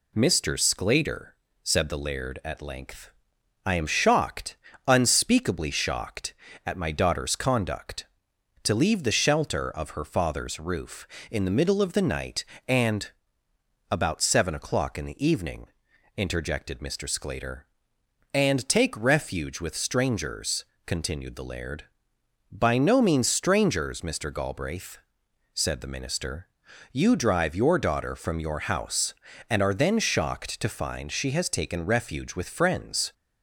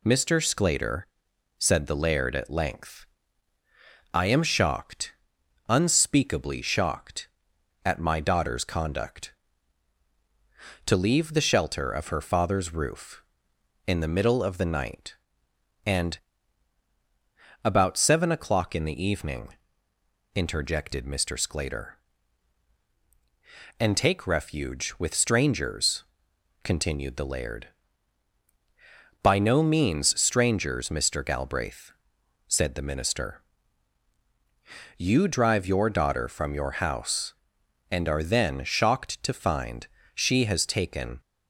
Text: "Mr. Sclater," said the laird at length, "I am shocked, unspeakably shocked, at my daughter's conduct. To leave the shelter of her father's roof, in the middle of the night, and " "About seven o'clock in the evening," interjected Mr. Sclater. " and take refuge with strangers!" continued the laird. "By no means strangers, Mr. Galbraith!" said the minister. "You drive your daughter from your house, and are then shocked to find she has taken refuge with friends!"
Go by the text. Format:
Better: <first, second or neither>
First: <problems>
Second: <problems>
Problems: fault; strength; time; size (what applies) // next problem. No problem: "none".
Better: first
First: none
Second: pauses between "find" and "she"; slight; at 39.8 s; 0.28 s long // stops before "refuge with friends"; at 41.2 s